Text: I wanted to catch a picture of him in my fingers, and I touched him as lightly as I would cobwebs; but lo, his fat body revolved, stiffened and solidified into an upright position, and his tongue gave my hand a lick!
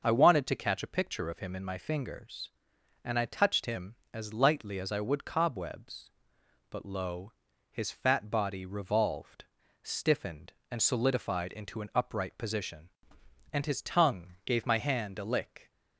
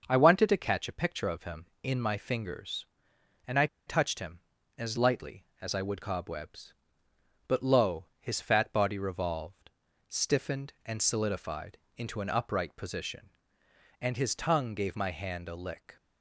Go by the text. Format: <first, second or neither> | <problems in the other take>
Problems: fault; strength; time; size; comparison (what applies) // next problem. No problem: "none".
first | starts louder than the rest; until 1.0 s; 6.5 dB; noticeable in the first // pauses between "I" and "touched"; slight; at 3.6 s; 0.20 s long // pauses between "solidified" and "into"; slight; at 11.7 s; 0.20 s long